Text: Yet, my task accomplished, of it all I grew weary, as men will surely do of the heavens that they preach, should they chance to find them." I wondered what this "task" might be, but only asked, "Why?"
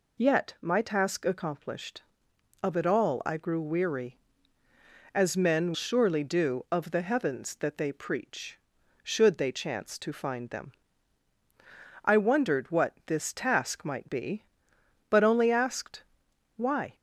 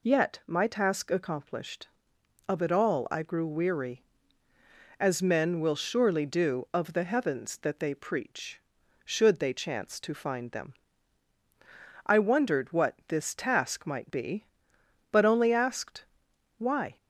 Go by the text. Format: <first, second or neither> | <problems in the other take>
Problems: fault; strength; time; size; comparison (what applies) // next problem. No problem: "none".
second | skips "will"; at 5.7 s